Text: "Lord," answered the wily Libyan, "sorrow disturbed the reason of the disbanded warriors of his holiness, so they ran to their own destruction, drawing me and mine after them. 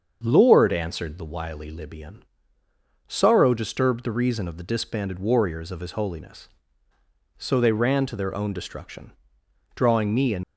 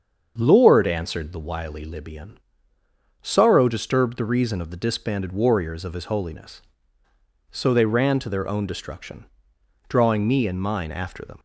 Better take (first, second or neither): second